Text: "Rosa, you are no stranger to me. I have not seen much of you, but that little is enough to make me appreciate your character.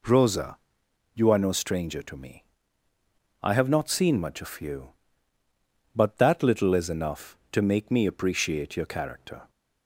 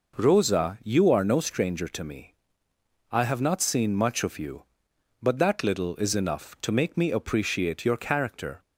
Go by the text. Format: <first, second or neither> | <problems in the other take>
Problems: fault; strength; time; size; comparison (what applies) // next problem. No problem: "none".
neither | none